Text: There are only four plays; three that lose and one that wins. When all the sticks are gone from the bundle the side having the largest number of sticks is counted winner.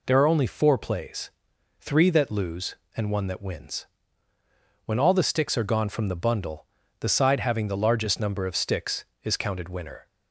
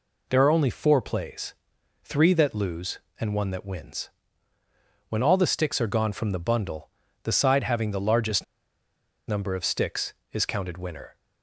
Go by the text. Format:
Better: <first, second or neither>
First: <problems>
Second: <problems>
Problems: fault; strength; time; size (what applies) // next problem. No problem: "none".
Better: first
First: pauses between "bundle" and "the"; slight; at 6.6 s; 0.34 s long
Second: pauses between "bundle" and "the"; slight; at 6.8 s; 0.34 s long // pauses between "largest" and "number"; noticeable; at 8.4 s; 0.83 s long